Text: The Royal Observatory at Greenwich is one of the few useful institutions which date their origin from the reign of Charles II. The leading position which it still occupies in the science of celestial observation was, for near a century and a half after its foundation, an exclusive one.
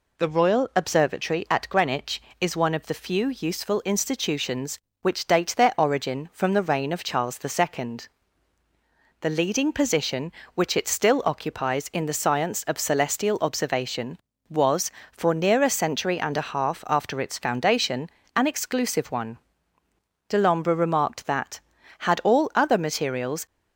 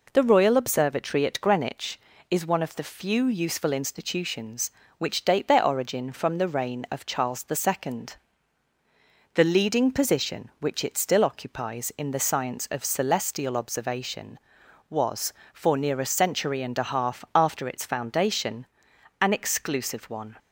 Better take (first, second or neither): second